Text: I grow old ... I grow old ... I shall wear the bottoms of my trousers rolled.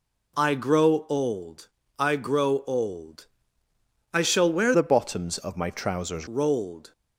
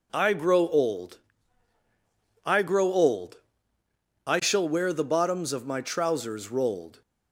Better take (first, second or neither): second